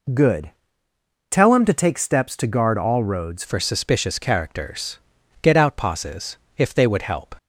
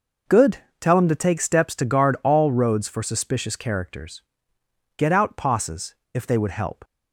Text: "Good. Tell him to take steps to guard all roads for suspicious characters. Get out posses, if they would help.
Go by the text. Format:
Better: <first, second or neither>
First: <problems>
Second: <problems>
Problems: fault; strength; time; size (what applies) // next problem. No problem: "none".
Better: second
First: changes voice at "for"; from 3.4 s on; 3.9 s long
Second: none